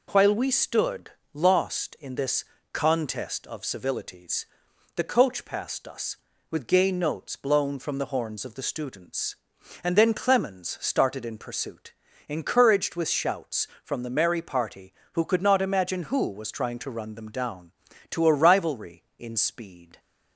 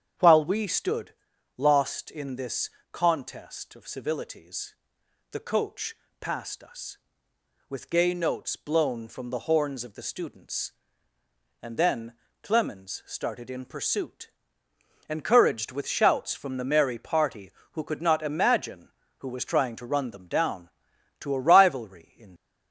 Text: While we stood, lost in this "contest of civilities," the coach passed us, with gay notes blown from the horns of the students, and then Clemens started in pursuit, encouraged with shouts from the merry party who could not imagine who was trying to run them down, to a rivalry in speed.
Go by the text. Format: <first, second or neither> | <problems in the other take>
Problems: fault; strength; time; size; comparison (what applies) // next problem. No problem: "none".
first | starts louder than the rest; strong; until 1.6 s; 8 dB // pauses between "this" and "contest"; slight; at 2.6 s; 0.24 s long; slight in the first // pauses between "coach" and "passed"; slight; at 5.9 s; 0.28 s long // pauses between "then" and "Clemens"; slight; at 12.1 s; 0.28 s long // stops before "speed"; at 22.3 s